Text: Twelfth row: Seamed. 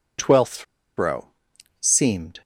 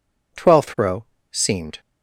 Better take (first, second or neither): second